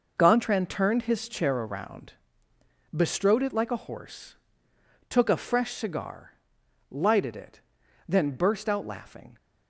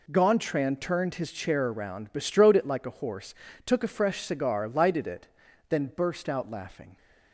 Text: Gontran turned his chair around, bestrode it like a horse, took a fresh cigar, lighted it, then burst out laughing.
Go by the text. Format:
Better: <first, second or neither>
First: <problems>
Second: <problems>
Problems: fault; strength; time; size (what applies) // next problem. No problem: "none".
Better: neither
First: none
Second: none